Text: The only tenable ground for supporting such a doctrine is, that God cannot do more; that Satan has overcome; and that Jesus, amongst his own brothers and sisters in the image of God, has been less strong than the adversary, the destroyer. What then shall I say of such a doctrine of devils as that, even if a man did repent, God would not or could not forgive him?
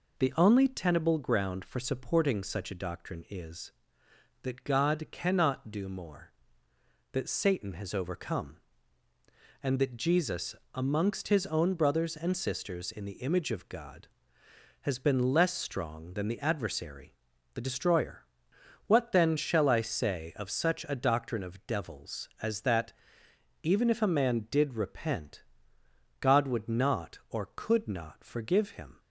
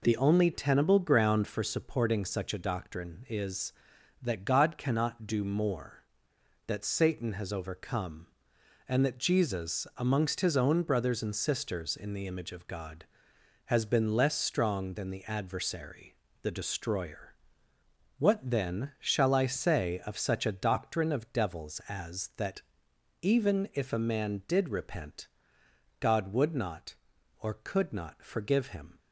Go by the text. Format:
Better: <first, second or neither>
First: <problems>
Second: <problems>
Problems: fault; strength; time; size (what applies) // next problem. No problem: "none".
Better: neither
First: none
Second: none